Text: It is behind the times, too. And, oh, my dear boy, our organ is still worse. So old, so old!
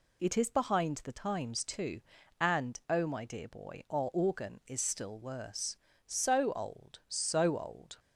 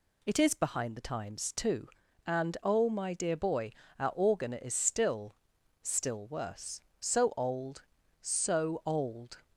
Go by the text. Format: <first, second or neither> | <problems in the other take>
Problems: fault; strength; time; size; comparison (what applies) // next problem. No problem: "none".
first | says "still" twice; at 5.8 s